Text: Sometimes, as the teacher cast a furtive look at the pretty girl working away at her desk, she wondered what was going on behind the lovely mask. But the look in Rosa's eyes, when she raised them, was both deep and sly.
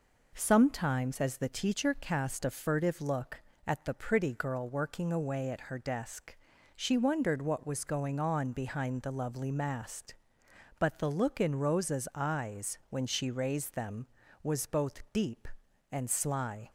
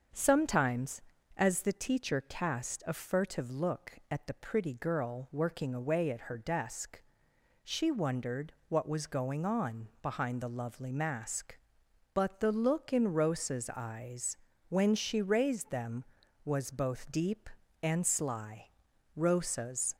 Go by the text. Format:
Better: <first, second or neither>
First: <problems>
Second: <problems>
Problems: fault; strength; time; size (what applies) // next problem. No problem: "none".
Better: first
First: none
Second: starts louder than the rest; until 1.5 s; 7 dB // pauses between "wondered" and "what"; slight; at 8.5 s; 0.16 s long // goes on to say "Rosa's"; noticeable; from 19.1 s on; 0.80 s long